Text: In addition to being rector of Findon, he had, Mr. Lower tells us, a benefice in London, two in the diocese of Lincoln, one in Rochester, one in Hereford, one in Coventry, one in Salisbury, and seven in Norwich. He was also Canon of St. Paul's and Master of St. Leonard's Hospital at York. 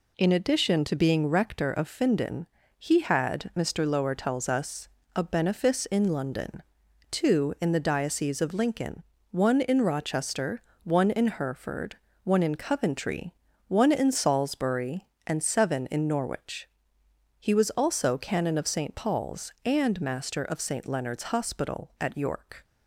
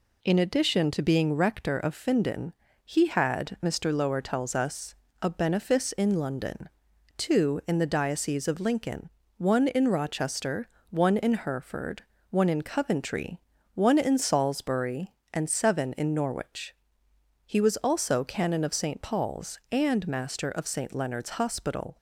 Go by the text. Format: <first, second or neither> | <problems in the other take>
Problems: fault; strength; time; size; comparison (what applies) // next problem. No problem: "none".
first | stops before "at York"; at 21.9 s